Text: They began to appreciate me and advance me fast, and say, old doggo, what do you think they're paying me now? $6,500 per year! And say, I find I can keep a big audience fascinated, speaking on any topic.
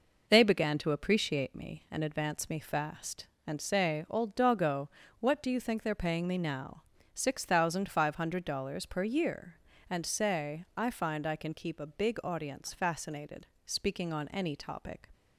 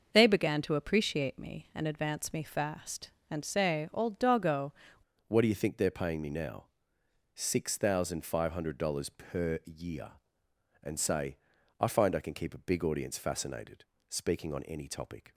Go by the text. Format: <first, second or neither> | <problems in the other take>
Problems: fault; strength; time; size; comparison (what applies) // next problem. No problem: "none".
first | starts louder than the rest; noticeable; until 1.1 s; 6 dB // changes voice at "what"; from 5.2 s on; 10.1 s long